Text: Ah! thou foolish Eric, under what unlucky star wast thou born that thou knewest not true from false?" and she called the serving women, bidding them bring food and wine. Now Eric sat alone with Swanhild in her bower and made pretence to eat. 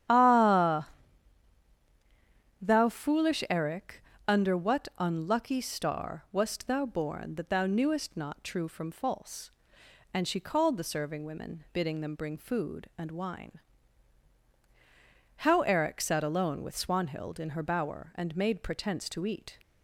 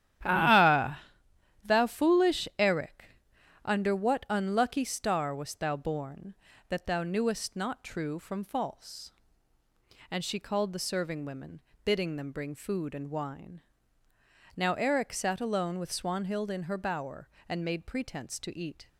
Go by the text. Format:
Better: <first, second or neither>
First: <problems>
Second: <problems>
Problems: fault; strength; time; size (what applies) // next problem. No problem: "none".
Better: second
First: starts louder than the rest; strong; until 2.8 s; 10.5 dB // says "How" for "Now"; at 15.3 s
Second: starts louder than the rest; strong; until 1.9 s; 12 dB